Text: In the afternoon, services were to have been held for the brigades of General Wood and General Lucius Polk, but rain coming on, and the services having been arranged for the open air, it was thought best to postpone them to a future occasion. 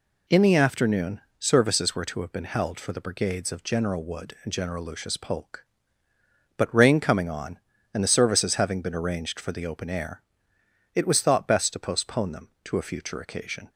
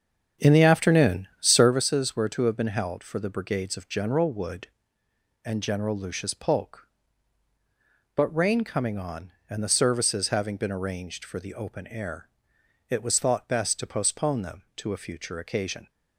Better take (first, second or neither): first